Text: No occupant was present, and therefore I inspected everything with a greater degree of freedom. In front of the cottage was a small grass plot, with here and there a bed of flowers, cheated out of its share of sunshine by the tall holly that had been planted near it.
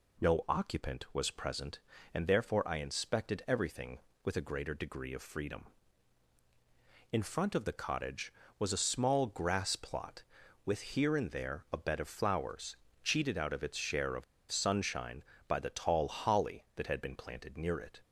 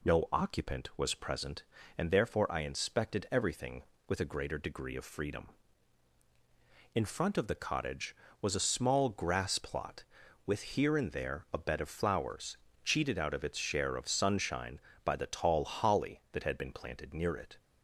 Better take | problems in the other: second | pauses between "of" and "sunshine"; slight; at 14.2 s; 0.26 s long

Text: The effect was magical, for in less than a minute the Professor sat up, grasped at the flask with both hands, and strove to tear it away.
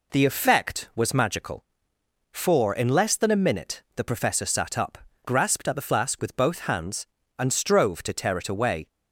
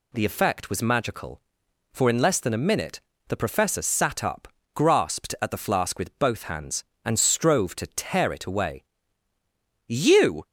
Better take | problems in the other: first | pauses between "minute" and "the"; slight; at 2.9 s; 0.28 s long // goes on to say "You"; from 9.8 s on; 0.60 s long

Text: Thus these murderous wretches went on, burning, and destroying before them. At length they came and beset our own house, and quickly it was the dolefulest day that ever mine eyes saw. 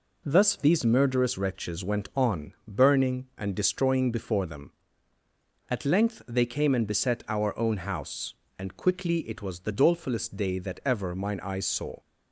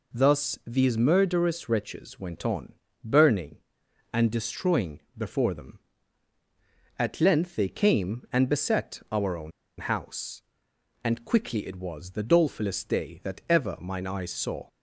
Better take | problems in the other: first | pauses between "destroying" and "before"; slight; at 4.9 s; 0.18 s long // pauses between "own" and "house"; slight; at 9.5 s; 0.28 s long

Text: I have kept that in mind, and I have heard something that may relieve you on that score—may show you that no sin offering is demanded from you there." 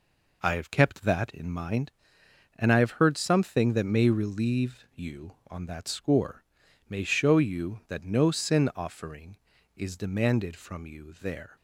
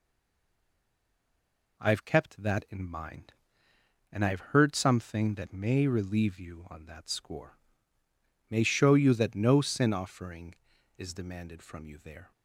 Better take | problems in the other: first | stays silent before the first word; noticeable; until 1.7 s; 1.7 s long

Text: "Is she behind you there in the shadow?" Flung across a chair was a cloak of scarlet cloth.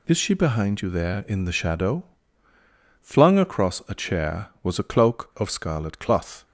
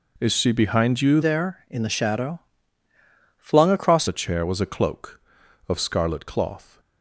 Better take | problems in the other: first | changes voice from "there" to "across"; from 1.2 to 4.0 s; 2.8 s long

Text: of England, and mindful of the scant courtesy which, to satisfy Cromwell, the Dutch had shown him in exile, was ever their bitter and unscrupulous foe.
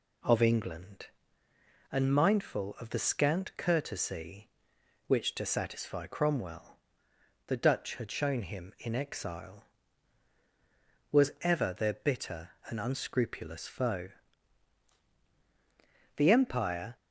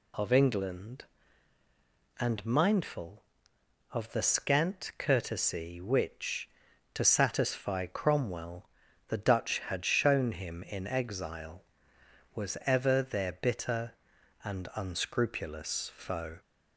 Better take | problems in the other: second | goes on to say "The empire"; noticeable; from 16.1 s on; 0.78 s long

